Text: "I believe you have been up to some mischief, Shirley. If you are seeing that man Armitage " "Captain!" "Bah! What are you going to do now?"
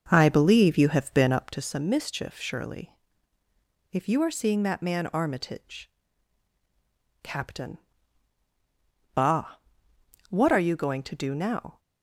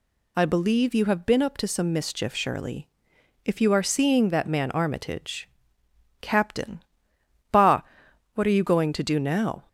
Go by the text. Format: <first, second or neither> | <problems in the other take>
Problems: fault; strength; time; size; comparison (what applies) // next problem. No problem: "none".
second | starts louder than the rest; until 1.6 s; 6.5 dB